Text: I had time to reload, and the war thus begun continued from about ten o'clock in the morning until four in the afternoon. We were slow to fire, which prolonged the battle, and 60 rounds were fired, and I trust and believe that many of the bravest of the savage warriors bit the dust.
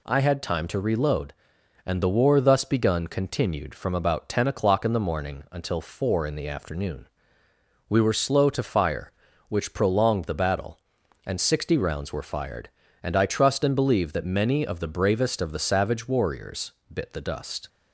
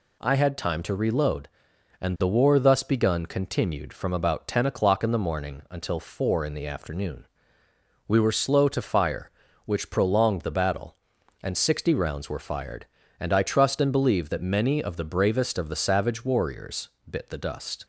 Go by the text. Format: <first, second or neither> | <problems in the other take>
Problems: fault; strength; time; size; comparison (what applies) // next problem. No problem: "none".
neither | pauses between "warriors" and "bit"; slight; the same in both